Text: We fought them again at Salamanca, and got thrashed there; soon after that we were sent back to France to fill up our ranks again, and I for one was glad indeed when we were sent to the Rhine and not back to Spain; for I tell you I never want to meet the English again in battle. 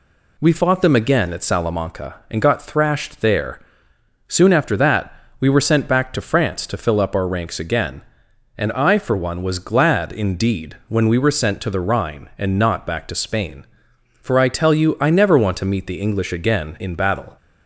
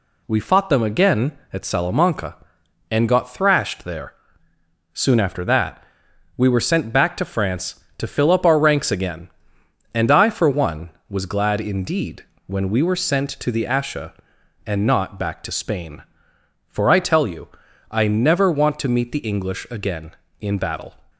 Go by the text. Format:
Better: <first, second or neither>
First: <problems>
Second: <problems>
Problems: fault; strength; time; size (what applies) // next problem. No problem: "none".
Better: first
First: pauses between "that" and "we"; slight; at 5.1 s; 0.28 s long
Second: pauses between "that" and "we"; noticeable; at 5.8 s; 0.54 s long // pauses between "indeed" and "when"; slight; at 12.2 s; 0.22 s long // says "Asha" for "Rhine"; at 13.6 s // pauses between "you" and "I"; at 17.4 s; 0.42 s long